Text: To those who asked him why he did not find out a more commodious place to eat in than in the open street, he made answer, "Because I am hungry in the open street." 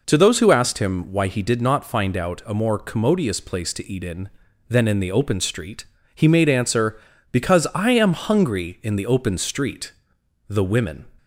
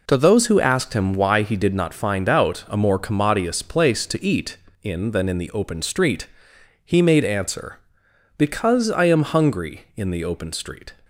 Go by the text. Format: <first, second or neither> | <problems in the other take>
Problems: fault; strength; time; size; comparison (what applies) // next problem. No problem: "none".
second | goes on to say "The women"; from 10.4 s on; 0.60 s long